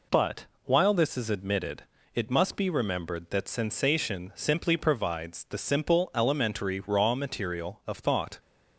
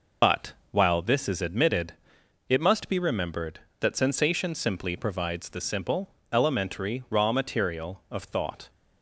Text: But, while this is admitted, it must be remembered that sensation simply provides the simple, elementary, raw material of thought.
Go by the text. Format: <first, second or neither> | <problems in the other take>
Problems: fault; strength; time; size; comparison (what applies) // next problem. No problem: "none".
first | loses the start of "But"; at 0.2 s; 80 ms